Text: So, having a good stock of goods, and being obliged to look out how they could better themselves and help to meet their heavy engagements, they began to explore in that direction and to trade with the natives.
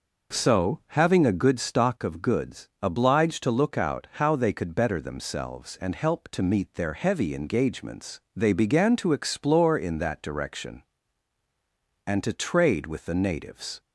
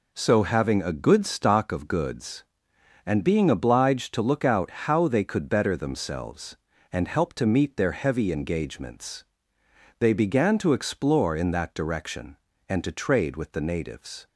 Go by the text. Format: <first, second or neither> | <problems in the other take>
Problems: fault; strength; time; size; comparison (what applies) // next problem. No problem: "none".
second | skips "and being"; at 2.7 s